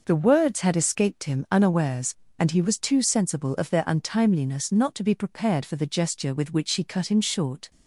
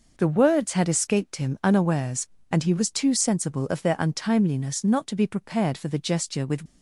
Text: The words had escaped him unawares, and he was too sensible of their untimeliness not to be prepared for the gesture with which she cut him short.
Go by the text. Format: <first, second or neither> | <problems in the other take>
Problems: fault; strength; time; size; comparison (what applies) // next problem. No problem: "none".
first | stops before "which she cut him short"; at 6.6 s